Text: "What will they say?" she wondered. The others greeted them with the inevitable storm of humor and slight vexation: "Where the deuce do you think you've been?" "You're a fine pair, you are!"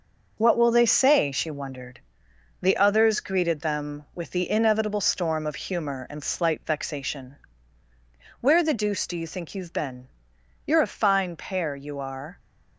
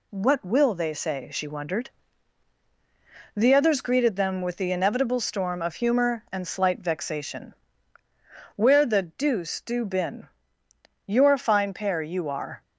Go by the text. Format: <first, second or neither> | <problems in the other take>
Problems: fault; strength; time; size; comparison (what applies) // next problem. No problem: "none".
first | skips "you think you've"; at 9.8 s